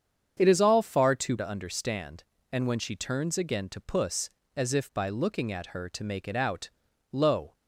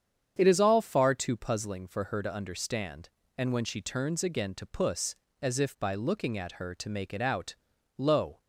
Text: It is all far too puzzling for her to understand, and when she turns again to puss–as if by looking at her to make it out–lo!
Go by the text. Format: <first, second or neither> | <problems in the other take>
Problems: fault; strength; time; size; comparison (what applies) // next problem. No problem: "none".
second | starts louder than the rest; strong; until 1.4 s; 7.5 dB; strong in the second // skips "puzzling for her"; at 1.3 s